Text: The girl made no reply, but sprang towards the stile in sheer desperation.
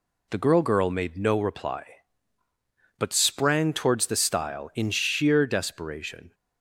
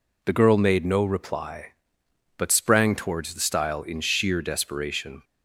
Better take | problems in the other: second | says "girl" twice; at 0.5 s

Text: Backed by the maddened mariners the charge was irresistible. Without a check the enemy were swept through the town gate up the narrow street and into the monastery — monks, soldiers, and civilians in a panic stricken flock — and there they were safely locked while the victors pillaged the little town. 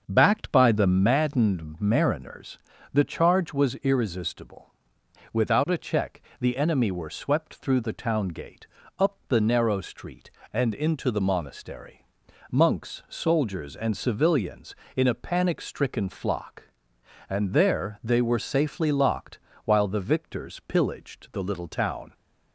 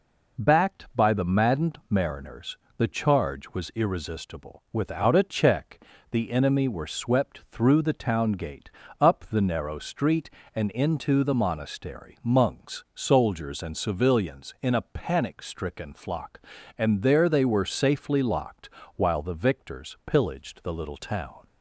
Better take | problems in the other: second | starts louder than the rest; until 1.2 s; 6.5 dB // pauses between "mariners" and "the"; slight; at 2.5 s; 0.34 s long; slight in the second // pauses between "check" and "the"; slight; at 6.2 s; 0.18 s long; slight in the second // pauses between "gate" and "up"; slight; at 8.6 s; 0.32 s long; slight in the second // pauses between "locked" and "while"; slight; at 19.3 s; 0.26 s long; slight in the second

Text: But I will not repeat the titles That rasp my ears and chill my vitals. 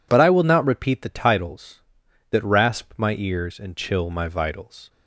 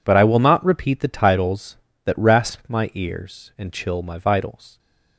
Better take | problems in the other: neither | none

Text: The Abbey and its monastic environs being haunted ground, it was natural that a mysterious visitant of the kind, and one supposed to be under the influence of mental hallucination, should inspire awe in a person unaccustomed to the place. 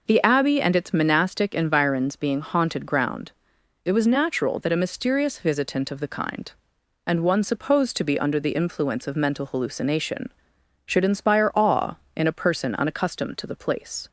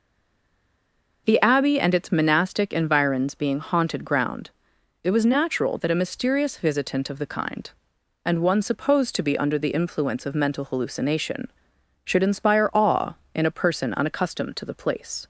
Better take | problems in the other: first | stays silent before the first word; noticeable; until 1.2 s; 1.2 s long

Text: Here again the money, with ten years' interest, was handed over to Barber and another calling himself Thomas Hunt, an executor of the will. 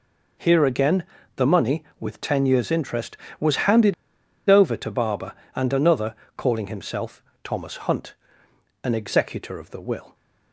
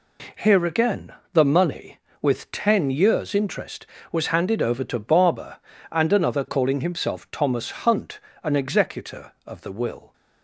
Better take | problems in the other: second | pauses between "again" and "the"; slight; at 1.0 s; 0.32 s long; slight in the second // pauses between "handed" and "over"; noticeable; at 3.9 s; 0.55 s long // pauses between "another" and "calling"; slight; at 6.1 s; 0.22 s long // pauses between "himself" and "Thomas"; slight; at 7.2 s; 0.22 s long

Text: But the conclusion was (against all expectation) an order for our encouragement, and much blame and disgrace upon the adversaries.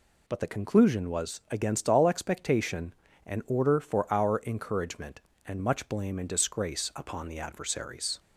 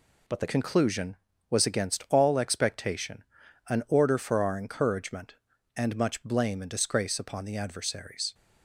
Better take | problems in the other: first | changes voice at "conclusion"; from 0.4 s on; 7.9 s long

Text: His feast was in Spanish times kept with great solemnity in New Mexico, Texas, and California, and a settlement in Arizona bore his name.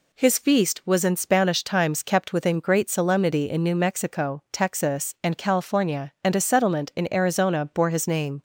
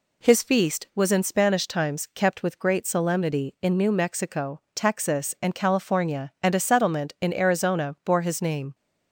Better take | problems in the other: second | says "within" for "with"; at 2.3 s

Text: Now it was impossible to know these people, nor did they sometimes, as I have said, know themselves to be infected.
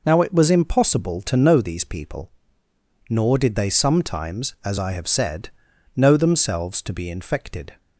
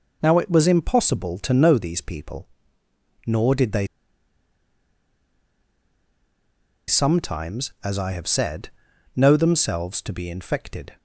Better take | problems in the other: first | pauses between "they" and "sometimes"; strong; at 3.8 s; 3.0 s long

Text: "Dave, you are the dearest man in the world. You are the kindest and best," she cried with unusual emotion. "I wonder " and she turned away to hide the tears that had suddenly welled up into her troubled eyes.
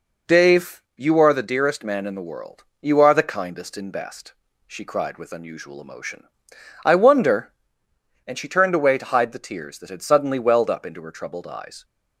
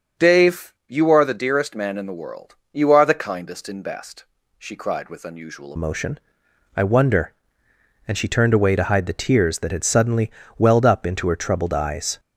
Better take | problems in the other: first | starts louder than the rest; strong; until 1.3 s; 7.5 dB // changes voice at "emotion"; from 5.7 s on; 6.4 s long // pauses between "suddenly" and "welled"; slight; at 10.2 s; 0.30 s long

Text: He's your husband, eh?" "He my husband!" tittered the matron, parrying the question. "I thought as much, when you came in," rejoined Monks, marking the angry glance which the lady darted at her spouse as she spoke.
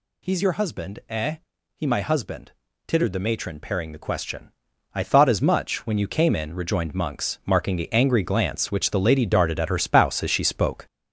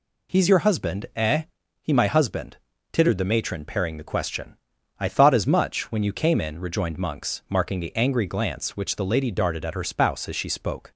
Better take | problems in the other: second | gets louder; noticeable; throughout; 5 dB

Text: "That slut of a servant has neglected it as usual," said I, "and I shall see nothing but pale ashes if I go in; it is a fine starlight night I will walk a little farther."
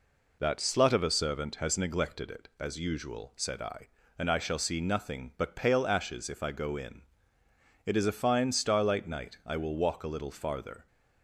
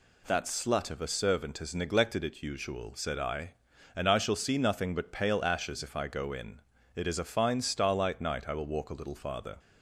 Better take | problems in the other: first | skips "as"; at 2.4 s

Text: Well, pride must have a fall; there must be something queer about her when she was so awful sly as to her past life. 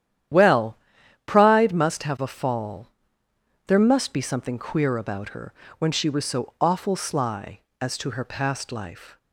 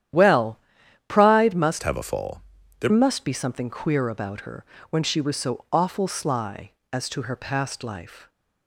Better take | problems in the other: first | starts louder than the rest; strong; until 1.6 s; 10.5 dB; strong in the first // changes voice from "have" to "there"; from 1.8 to 2.9 s; 1.1 s long // pauses between "her" and "when"; slight; at 4.6 s; 0.26 s long; slight in the first

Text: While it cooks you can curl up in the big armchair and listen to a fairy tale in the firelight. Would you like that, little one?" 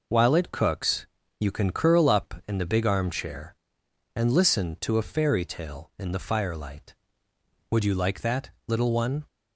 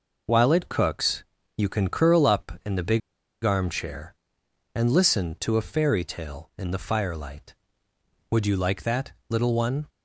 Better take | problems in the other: first | pauses between "cooks" and "you"; slight; at 1.2 s; 0.34 s long; slight in the first // pauses between "big" and "armchair"; at 3.0 s; 0.43 s long

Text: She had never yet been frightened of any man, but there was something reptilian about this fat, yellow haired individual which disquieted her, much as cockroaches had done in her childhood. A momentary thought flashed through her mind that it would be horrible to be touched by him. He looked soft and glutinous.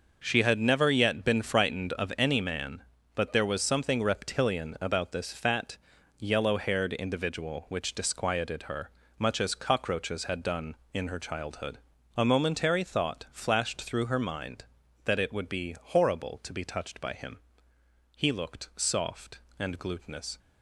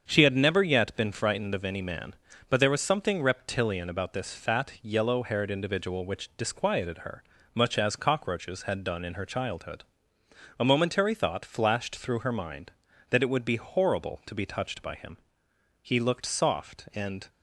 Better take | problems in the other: first | starts louder than the rest; strong; until 1.0 s; 7 dB // stops before "glutinous"; at 17.2 s

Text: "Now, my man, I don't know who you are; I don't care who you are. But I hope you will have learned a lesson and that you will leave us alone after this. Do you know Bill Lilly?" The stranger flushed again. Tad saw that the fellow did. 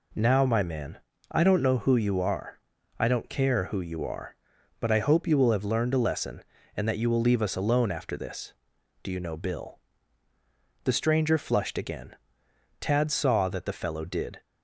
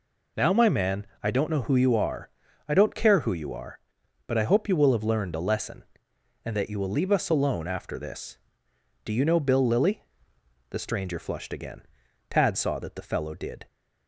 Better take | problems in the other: second | skips "Lilly"; at 10.3 s

